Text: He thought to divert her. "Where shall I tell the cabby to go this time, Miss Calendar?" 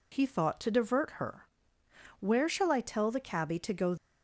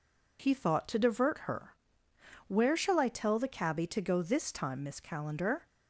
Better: second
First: stops before "this time Miss Calendar"; at 3.9 s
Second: none

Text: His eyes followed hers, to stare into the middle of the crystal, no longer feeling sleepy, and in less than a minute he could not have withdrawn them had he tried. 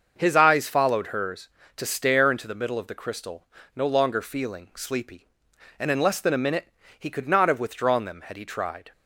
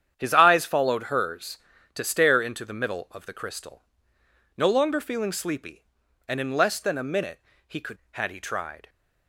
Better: first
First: starts louder than the rest; until 1.1 s; 6.5 dB // pauses between "minute" and "he"; slight; at 6.7 s; 0.26 s long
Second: starts louder than the rest; strong; until 1.1 s; 9 dB // pauses between "minute" and "he"; slight; at 7.4 s; 0.26 s long // skips "not have withdrawn them"; at 8.0 s

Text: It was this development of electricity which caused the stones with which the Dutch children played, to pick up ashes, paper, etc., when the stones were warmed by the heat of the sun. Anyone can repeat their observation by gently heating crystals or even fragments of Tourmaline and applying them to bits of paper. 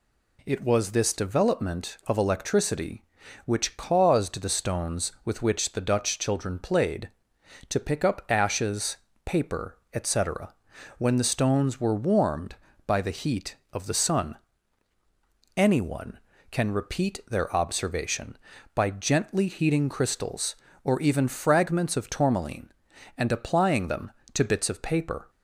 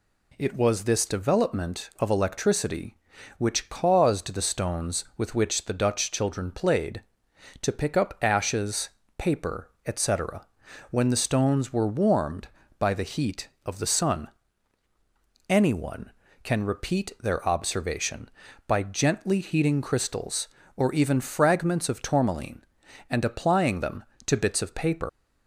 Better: first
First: none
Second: leaves "paper" unfinished; at 25.0 s; 130 ms

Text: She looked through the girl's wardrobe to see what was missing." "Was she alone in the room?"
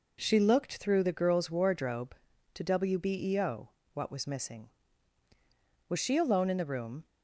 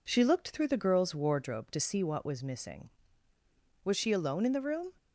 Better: second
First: says "wbeo" for "see"; at 2.6 s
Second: none

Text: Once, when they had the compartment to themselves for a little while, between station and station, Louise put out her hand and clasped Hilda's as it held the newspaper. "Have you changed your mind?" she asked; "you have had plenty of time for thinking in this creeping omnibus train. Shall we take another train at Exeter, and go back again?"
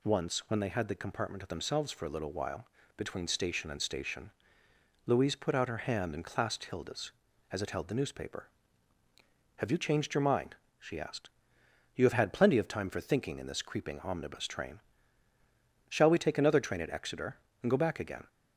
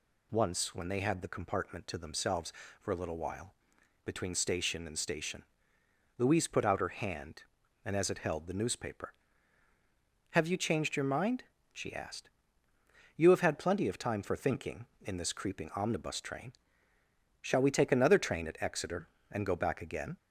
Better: first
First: none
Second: skips "clasped Hilda's"; at 7.9 s

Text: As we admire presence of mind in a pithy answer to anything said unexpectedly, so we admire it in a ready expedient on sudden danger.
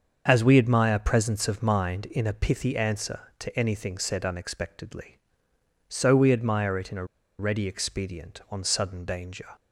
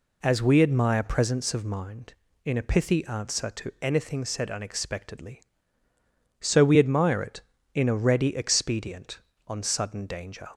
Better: second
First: starts louder than the rest; until 1.2 s; 7 dB // pauses between "a" and "ready"; slight; at 7.0 s; 0.34 s long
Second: none

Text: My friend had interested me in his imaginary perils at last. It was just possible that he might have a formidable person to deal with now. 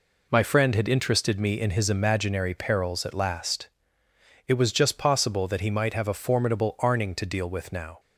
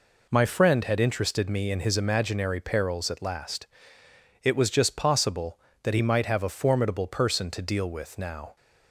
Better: second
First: says "arning" for "person"; at 6.7 s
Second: none

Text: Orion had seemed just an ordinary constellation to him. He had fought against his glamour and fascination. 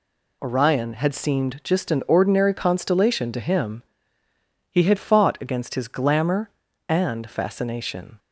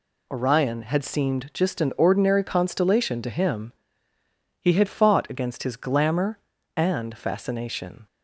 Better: neither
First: none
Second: none

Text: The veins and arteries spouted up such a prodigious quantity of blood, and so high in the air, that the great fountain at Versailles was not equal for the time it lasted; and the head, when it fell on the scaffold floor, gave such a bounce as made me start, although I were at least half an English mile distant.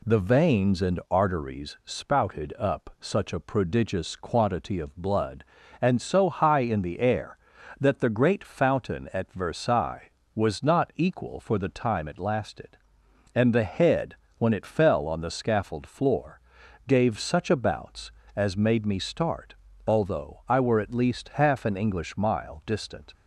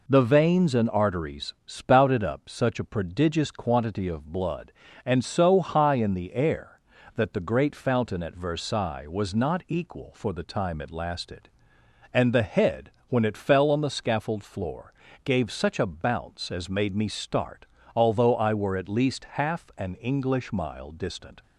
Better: neither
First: none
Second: none

